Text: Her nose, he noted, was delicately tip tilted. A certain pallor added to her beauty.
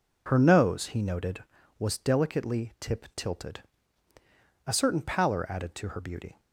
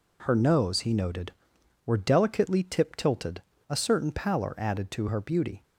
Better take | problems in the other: first | says "were" for "was"; at 1.8 s

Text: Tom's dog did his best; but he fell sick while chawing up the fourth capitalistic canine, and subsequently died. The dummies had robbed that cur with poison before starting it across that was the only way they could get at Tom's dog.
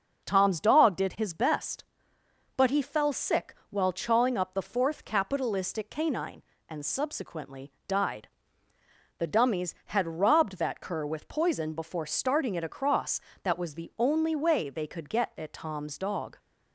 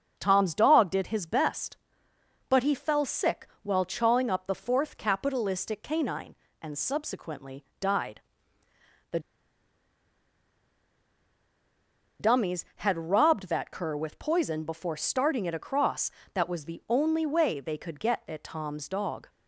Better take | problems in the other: first | starts louder than the rest; noticeable; until 1.1 s; 6 dB; also in the first // pauses between "sick" and "while"; slight; at 3.4 s; 0.16 s long; slight in the first // pauses between "subsequently" and "died"; slight; at 7.6 s; 0.16 s long; slight in the first // pauses between "The" and "dummies"; strong; at 9.1 s; 3.0 s long

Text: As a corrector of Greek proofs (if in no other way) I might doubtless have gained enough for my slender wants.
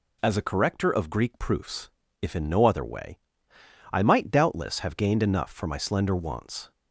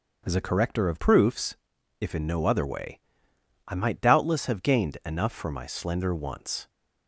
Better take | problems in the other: first | starts louder than the rest; until 1.2 s; 6.5 dB // skips "Greek"; at 0.9 s

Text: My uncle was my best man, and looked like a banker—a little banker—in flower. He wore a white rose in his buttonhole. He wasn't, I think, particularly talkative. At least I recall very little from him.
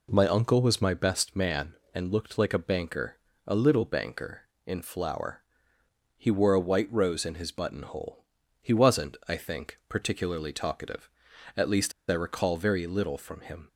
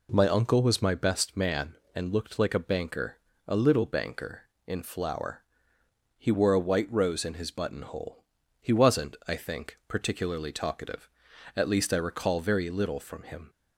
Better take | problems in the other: second | pauses between "least" and "I"; slight; at 11.9 s; 0.17 s long

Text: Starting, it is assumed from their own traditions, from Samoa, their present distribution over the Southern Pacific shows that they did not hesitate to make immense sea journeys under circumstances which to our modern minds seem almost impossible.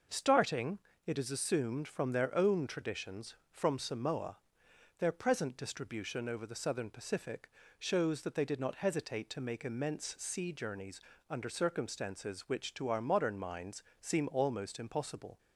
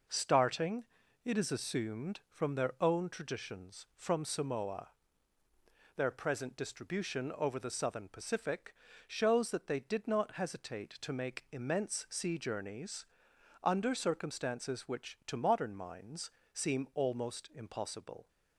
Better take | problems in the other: first | pauses between "Pacific" and "shows"; slight; at 8.7 s; 0.32 s long; slight in the first // pauses between "journeys" and "under"; noticeable; at 13.0 s; 0.60 s long; slight in the first // skips "our"; at 15.3 s // pauses between "minds" and "seem"; slight; at 16.2 s; 0.24 s long; slight in the first

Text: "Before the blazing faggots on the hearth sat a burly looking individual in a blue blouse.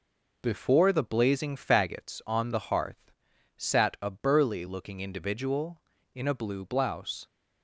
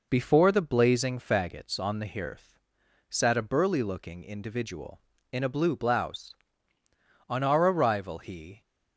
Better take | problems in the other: first | pauses between "hearth" and "sat"; noticeable; at 2.5 s; 0.52 s long; noticeable in the first // goes on to say "On our arrival he"; from 7.2 s on; 1.3 s long

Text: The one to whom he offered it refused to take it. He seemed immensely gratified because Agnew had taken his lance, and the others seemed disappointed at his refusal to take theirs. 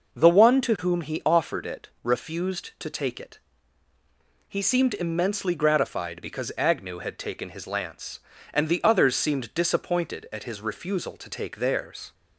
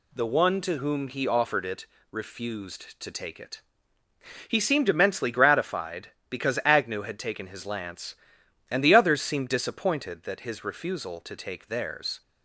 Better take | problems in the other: first | pauses between "it" and "refused"; slight; at 1.8 s; 0.26 s long; slight in the first // says "that" for "at"; at 10.2 s

